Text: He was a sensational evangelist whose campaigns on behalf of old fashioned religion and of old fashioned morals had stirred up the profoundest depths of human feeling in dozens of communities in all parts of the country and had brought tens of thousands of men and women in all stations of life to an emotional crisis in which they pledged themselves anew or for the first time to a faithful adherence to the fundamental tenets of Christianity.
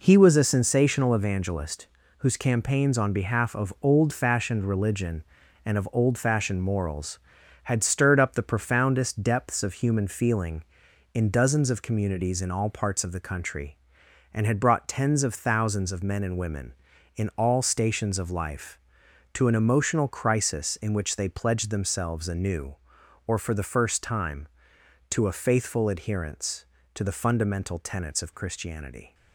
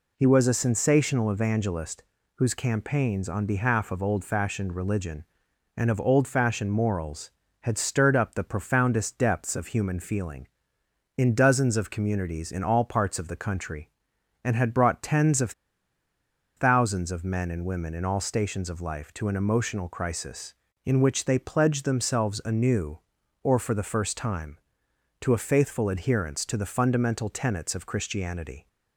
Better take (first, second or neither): first